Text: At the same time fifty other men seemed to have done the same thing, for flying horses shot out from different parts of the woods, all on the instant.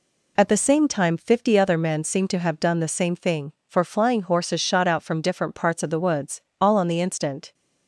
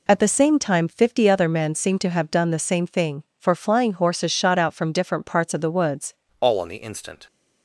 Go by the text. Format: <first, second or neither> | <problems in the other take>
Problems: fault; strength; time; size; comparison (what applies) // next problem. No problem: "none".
first | changes voice at "all"; from 6.4 s on; 0.8 s long